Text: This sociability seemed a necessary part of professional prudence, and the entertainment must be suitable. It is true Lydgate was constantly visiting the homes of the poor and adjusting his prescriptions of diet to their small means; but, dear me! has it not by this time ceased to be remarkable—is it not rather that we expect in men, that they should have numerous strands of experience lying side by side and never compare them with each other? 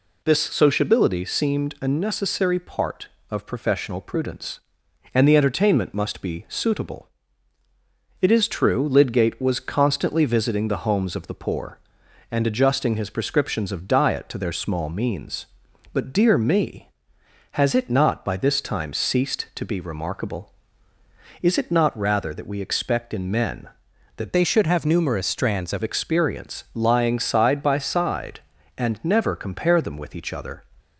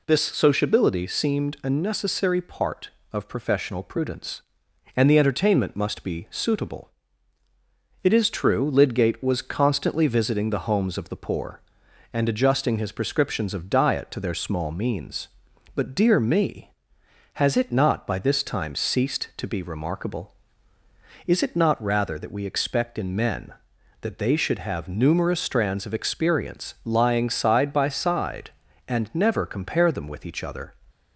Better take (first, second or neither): second